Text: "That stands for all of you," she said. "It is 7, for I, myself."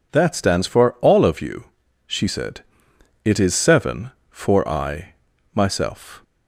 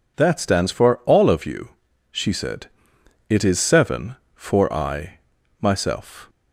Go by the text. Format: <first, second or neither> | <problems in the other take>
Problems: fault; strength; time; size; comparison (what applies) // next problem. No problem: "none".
neither | none